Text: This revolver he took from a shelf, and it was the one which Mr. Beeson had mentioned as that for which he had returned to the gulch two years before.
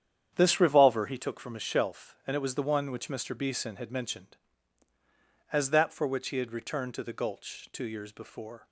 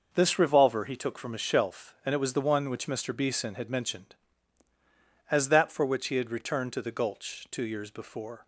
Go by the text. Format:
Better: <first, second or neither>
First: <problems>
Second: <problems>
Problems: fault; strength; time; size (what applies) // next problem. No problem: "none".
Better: second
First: starts louder than the rest; strong; until 1.4 s; 9 dB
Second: none